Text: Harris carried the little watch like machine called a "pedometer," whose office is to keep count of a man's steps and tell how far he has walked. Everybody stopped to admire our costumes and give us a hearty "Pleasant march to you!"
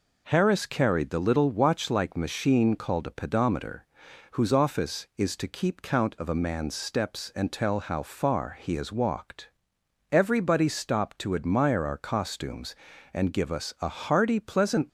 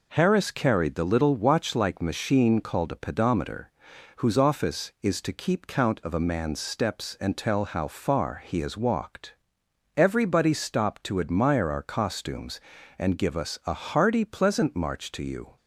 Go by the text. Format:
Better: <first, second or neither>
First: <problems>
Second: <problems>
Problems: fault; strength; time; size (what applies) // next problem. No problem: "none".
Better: second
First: stops before "march to you"; at 14.8 s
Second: none